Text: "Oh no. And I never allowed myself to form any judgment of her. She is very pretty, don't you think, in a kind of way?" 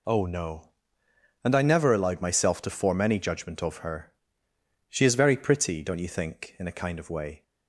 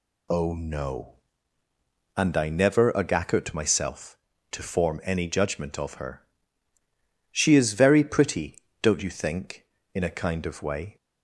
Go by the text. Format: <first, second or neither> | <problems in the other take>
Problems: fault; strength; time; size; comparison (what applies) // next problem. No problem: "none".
first | says "agakut" for "allowed"; at 2.9 s